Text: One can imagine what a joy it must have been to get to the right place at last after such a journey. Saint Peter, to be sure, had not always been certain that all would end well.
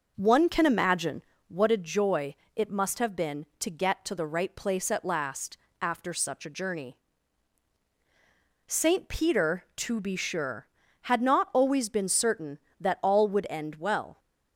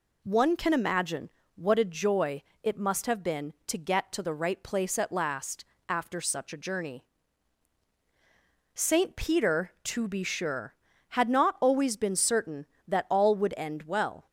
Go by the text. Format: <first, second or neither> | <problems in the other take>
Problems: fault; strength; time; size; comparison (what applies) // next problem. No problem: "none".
second | starts louder than the rest; noticeable; until 1.5 s; 5.5 dB // pauses between "imagine" and "what"; slight; at 1.2 s; 0.26 s long; slight in the second // pauses between "joy" and "it"; slight; at 2.3 s; 0.20 s long; slight in the second // pauses between "last" and "after"; slight; at 5.5 s; 0.24 s long; slight in the second